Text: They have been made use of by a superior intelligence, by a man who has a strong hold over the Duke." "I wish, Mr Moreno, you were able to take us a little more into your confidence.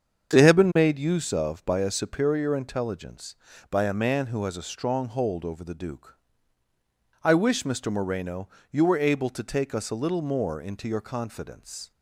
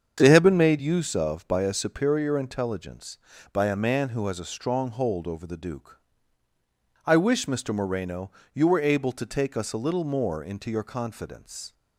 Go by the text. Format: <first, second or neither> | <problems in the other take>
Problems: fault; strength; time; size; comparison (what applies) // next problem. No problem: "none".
neither | starts louder than the rest; strong; the same in both